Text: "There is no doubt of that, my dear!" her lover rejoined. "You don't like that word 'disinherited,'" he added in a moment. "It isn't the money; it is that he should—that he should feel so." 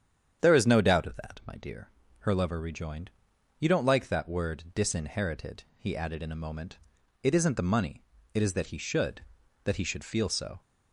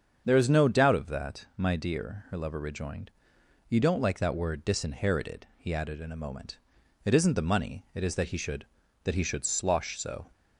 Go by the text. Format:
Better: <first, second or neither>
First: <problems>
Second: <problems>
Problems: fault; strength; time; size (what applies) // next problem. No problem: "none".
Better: first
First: starts louder than the rest; strong; until 1.4 s; 8.5 dB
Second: starts louder than the rest; strong; until 1.2 s; 7 dB // says "slosh" for "feel"; at 9.4 s